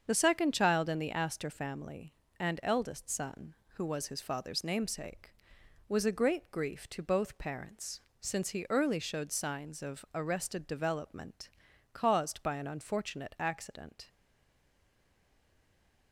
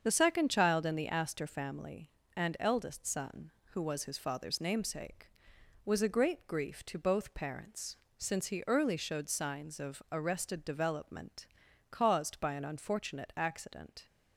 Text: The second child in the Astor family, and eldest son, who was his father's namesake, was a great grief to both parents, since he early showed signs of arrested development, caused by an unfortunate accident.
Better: second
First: starts louder than the rest; strong; until 1.0 s; 7 dB // stays silent after the last word; noticeable; from 14.0 s on; 2.1 s long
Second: starts louder than the rest; strong; until 1.0 s; 7 dB

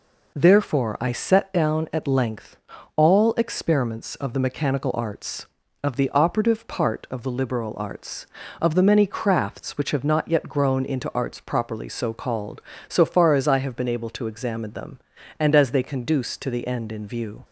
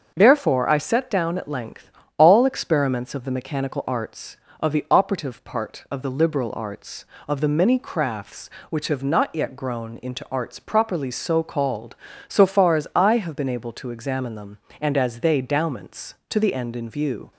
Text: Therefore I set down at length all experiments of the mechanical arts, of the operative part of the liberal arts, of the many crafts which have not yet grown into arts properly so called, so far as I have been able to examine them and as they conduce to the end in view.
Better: first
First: pauses between "length" and "all"; at 2.5 s; 0.38 s long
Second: starts louder than the rest; until 1.1 s; 6 dB // pauses between "length" and "all"; slight; at 1.8 s; 0.30 s long // says "dowments" for "conduce"; at 15.4 s

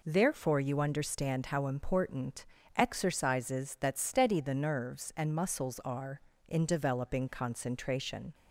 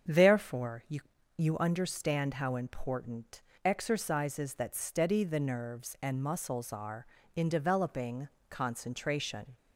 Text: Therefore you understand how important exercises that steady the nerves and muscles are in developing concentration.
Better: first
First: pauses between "important" and "exercises"; slight; at 2.4 s; 0.32 s long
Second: starts louder than the rest; strong; until 1.4 s; 7.5 dB // says "you" twice; at 1.3 s // pauses between "important" and "exercises"; slight; at 3.4 s; 0.24 s long // pauses between "developing" and "concentration"; slight; at 8.2 s; 0.20 s long

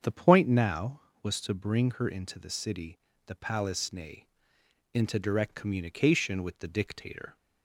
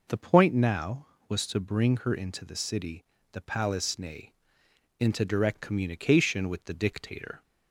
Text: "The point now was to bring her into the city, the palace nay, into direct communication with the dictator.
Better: second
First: starts louder than the rest; strong; until 1.1 s; 7.5 dB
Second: none

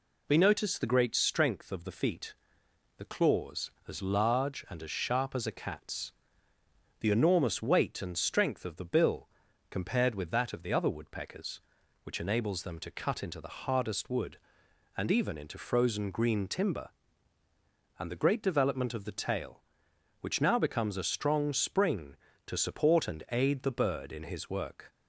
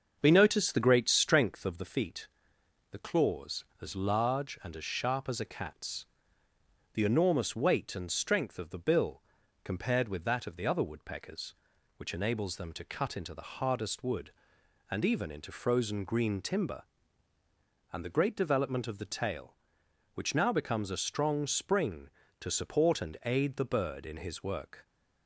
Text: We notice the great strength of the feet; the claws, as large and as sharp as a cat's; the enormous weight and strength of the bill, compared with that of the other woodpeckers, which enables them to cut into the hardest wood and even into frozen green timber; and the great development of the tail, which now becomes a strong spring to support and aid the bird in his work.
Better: first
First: none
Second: starts louder than the rest; until 1.9 s; 6.5 dB

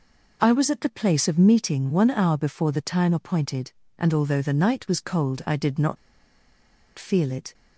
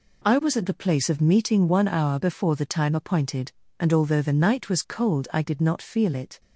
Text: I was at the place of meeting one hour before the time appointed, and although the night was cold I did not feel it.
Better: second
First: pauses between "not" and "feel"; at 5.9 s; 1.0 s long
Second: none

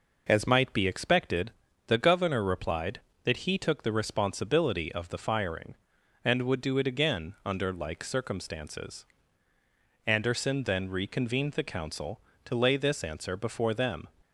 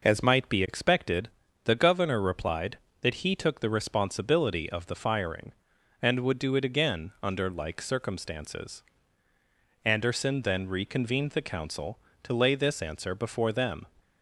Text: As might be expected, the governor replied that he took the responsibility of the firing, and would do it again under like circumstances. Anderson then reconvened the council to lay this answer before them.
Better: neither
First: none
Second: none

